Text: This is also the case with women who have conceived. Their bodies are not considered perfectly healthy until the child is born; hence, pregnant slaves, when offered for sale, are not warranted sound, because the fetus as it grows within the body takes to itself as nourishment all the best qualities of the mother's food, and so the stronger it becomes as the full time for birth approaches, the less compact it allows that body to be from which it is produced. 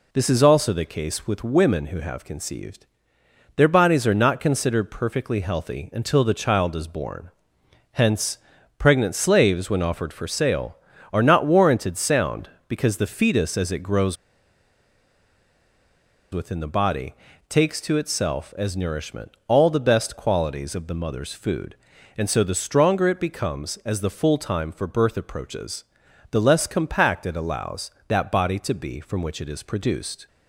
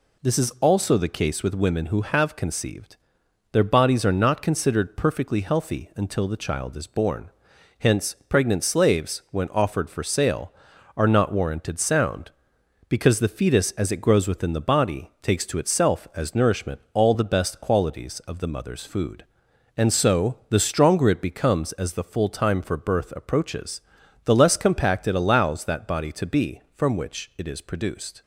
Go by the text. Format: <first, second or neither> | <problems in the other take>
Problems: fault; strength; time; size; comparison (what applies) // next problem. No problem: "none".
second | pauses between "grows" and "within"; strong; at 14.1 s; 2.1 s long // pauses between "body" and "takes"; slight; at 17.1 s; 0.32 s long // pauses between "nourishment" and "all"; slight; at 19.3 s; 0.16 s long